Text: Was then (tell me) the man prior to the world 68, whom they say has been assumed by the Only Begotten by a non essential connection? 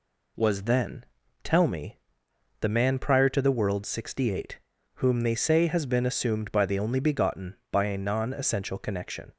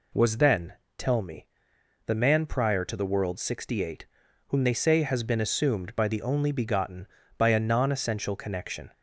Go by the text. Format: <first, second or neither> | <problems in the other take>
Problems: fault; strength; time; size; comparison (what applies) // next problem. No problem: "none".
neither | none